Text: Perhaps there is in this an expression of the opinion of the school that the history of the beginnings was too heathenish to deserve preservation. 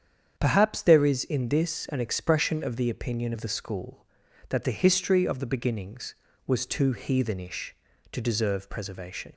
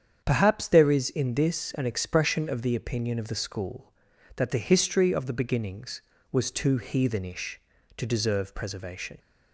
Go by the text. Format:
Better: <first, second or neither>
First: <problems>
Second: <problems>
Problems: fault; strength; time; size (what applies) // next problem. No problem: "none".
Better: neither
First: starts louder than the rest; strong; until 1.4 s; 8 dB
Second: starts louder than the rest; strong; until 1.2 s; 8 dB